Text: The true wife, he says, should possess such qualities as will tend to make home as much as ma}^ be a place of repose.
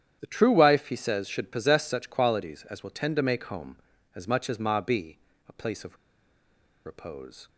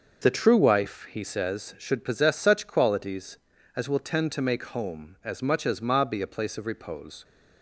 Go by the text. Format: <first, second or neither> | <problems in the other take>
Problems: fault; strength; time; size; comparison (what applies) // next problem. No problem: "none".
second | starts louder than the rest; strong; until 1.2 s; 9.5 dB; noticeable in the second // pauses between "be" and "a"; slight; at 5.1 s; 0.30 s long // pauses between "of" and "repose"; noticeable; at 5.9 s; 0.89 s long